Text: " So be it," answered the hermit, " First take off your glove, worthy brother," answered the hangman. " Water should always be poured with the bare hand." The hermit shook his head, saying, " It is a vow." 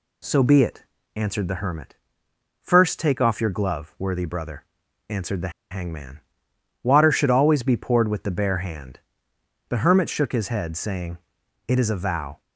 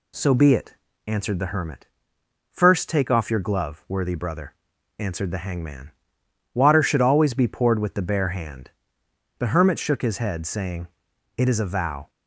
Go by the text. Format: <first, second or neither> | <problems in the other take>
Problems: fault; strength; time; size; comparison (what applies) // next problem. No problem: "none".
second | pauses between "the" and "hangman"; slight; at 5.5 s; 0.19 s long